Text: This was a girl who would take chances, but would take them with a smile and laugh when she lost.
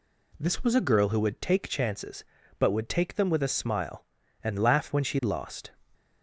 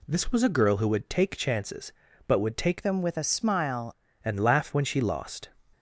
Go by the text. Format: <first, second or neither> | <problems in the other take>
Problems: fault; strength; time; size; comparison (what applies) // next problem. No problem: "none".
first | changes voice from "them" to "smile"; from 2.8 to 3.9 s; 1.1 s long